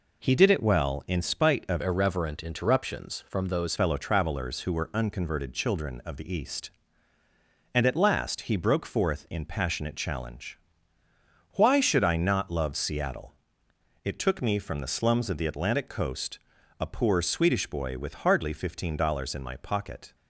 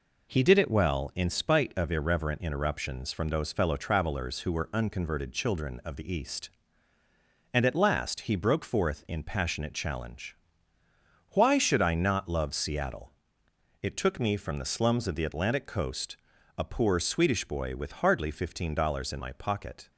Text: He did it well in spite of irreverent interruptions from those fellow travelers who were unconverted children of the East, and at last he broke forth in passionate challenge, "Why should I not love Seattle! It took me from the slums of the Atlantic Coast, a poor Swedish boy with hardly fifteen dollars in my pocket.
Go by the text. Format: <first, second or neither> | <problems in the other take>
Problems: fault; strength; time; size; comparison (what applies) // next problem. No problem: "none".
second | changes voice from "irreverent" to "those"; from 1.8 to 3.7 s; 1.9 s long